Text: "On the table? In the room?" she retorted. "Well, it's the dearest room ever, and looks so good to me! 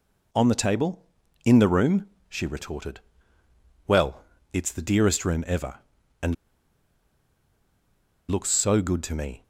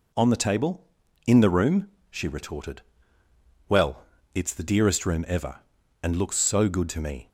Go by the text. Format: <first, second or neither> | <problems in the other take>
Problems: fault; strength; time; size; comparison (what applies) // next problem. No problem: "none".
second | pauses between "and" and "looks"; strong; at 6.3 s; 1.9 s long